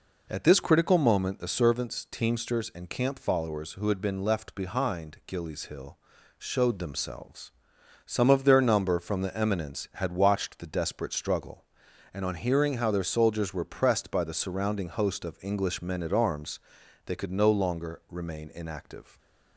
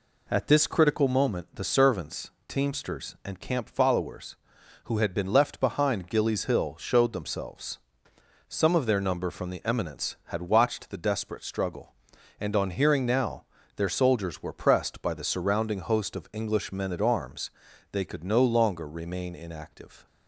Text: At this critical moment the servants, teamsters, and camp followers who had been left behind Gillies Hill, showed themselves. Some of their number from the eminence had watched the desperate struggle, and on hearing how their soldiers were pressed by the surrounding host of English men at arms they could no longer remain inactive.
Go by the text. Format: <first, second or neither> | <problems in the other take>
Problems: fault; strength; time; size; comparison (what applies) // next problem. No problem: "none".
first | says "now" for "how"; at 13.0 s // pauses between "arms" and "they"; at 17.4 s; 0.42 s long; noticeable in the first